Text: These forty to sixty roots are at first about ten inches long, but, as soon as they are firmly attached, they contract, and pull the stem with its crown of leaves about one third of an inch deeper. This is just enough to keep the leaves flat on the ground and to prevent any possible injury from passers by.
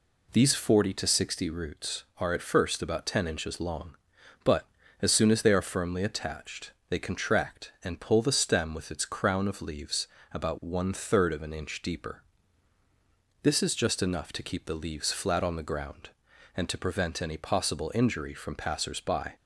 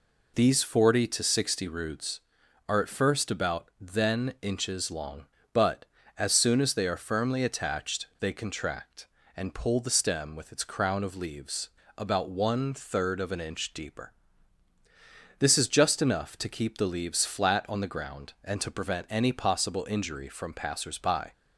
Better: first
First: pauses between "leaves" and "about"; slight; at 10.0 s; 0.26 s long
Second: says "then" for "ten"; at 3.7 s // pauses between "leaves" and "about"; slight; at 11.7 s; 0.28 s long

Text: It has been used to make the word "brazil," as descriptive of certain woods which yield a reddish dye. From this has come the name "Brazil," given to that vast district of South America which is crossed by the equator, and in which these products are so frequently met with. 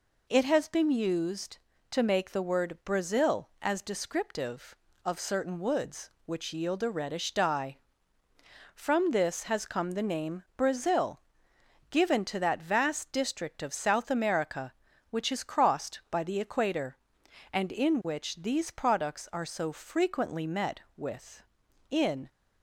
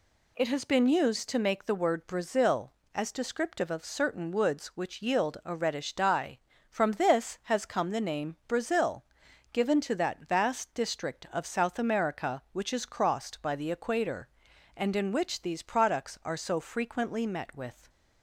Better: second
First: goes on to say "In"; slight; from 21.9 s on; 0.38 s long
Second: none

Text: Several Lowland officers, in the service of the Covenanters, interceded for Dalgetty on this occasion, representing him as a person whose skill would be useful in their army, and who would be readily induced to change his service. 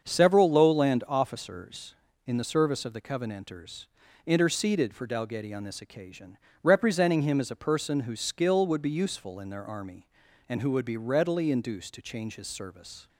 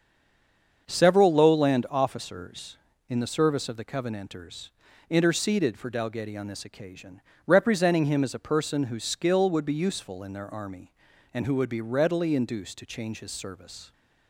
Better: first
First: starts louder than the rest; until 1.0 s; 7 dB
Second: stays silent before the first word; slight; until 0.8 s; 0.8 s long // starts louder than the rest; until 1.8 s; 7 dB

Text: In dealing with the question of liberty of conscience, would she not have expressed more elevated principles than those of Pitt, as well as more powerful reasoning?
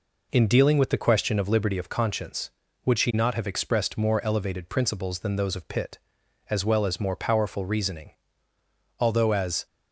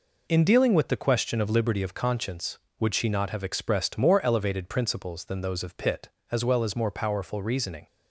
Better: second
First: goes on to say "Although as"; noticeable; from 8.9 s on; 0.68 s long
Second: none

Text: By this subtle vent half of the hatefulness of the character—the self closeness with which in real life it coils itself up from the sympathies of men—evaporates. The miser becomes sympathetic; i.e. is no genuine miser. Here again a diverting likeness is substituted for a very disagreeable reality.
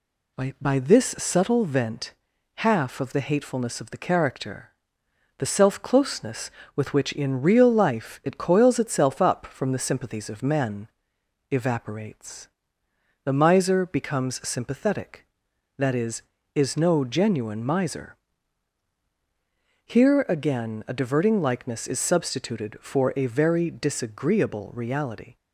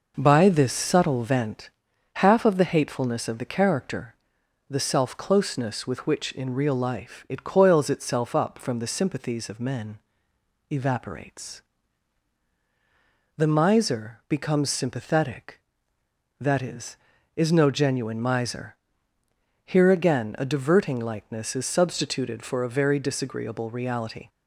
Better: second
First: says "By" twice; at 0.6 s // pauses between "vent" and "half"; at 2.1 s; 0.44 s long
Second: pauses between "vent" and "half"; noticeable; at 1.7 s; 0.46 s long

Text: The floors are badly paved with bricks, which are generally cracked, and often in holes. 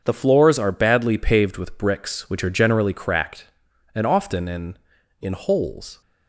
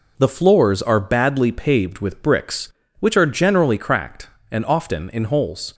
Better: second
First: starts louder than the rest; until 1.0 s; 6.5 dB // says "in" twice; at 5.2 s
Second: none

